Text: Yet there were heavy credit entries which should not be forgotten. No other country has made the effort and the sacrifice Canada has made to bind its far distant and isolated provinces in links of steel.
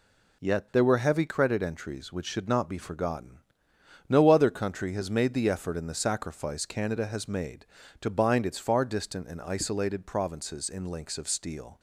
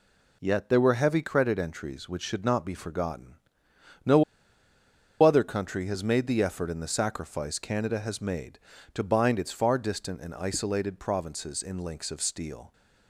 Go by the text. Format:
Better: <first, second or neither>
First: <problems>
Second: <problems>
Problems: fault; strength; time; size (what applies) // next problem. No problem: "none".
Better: first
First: none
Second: pauses between "No" and "other"; at 4.2 s; 0.98 s long